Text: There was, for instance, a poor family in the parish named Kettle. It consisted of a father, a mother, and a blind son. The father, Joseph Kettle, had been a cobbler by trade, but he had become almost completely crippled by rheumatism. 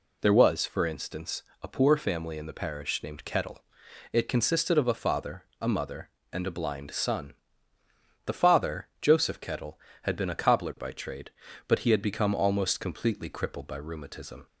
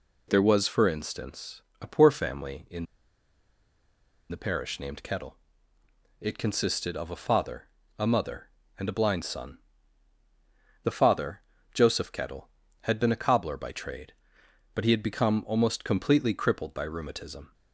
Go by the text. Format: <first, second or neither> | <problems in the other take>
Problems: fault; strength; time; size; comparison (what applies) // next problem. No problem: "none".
first | pauses between "in" and "the"; strong; at 2.8 s; 1.4 s long